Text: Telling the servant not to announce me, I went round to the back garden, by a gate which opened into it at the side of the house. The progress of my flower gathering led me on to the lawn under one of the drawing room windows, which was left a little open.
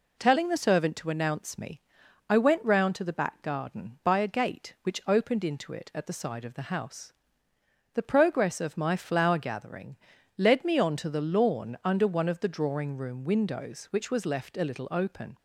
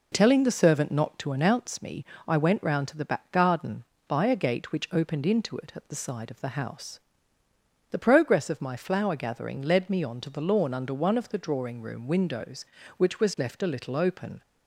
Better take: second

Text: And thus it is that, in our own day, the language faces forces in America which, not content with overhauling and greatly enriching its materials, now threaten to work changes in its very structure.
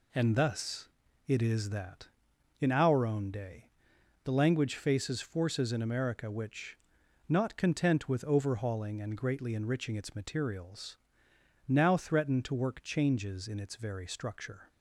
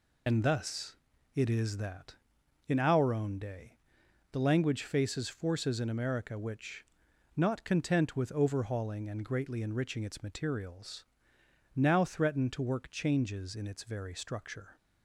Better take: first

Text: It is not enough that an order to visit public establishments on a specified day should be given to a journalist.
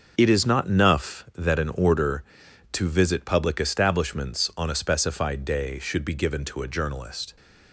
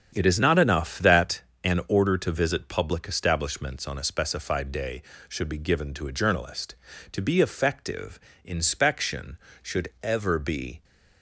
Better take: first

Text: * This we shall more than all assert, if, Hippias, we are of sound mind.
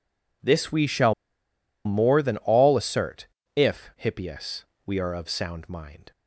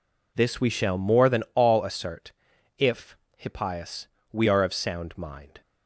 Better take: second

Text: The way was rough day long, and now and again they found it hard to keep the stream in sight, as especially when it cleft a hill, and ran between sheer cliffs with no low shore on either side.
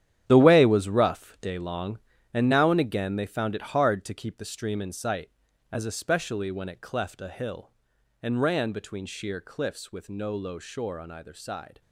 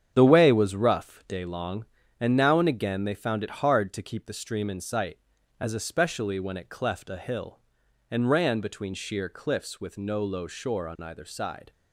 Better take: second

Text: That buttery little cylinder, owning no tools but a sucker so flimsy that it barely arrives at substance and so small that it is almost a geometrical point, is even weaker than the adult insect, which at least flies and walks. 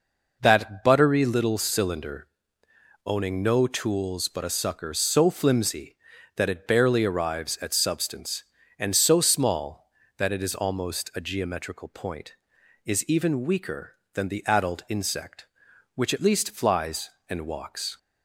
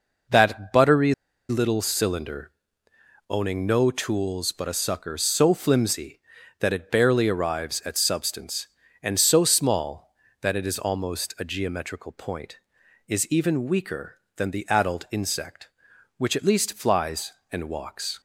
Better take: first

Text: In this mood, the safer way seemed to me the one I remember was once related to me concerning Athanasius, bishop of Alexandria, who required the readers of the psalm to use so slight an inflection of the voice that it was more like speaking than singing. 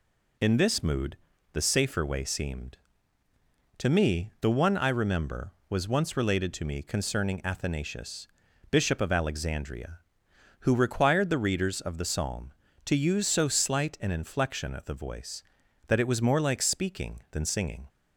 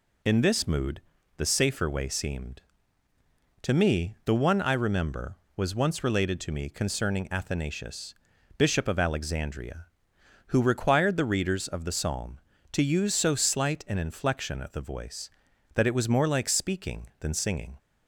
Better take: neither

